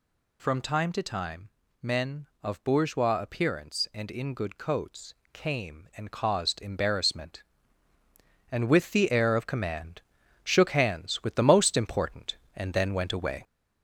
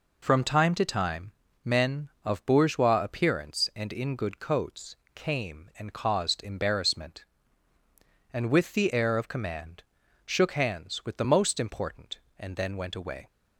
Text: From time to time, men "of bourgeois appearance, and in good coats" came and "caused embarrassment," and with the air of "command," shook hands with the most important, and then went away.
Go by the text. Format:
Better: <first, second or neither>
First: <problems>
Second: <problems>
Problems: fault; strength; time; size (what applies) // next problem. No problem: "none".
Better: second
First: gets louder; throughout; 3.5 dB // pauses between "coats" and "came"; slight; at 5.1 s; 0.20 s long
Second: pauses between "coats" and "came"; slight; at 4.9 s; 0.20 s long